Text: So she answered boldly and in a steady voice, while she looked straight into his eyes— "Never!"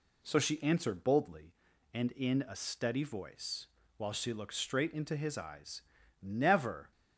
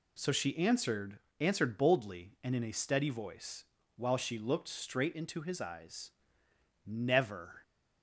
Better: first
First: none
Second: says "answered" twice; at 1.3 s

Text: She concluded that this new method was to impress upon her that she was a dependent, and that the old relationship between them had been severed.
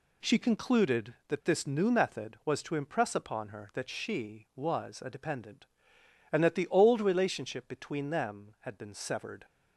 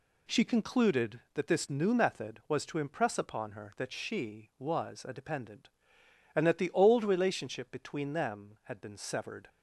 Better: neither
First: none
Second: none

